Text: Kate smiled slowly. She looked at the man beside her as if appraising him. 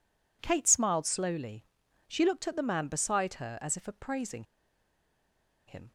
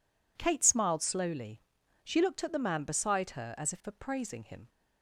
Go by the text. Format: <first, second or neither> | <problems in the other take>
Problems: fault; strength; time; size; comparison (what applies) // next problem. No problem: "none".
second | pauses between "appraising" and "him"; at 4.4 s; 1.2 s long